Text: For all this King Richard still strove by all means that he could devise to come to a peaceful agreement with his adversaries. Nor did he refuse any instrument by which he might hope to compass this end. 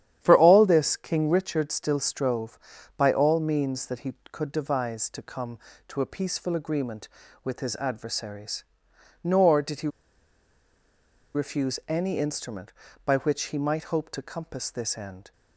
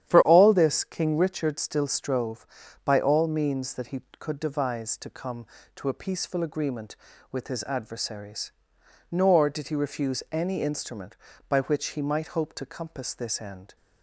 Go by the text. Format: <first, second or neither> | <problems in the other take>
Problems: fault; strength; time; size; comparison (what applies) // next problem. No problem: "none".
second | starts louder than the rest; strong; until 1.2 s; 10.5 dB; strong in the second // pauses between "he" and "refuse"; strong; at 9.8 s; 1.4 s long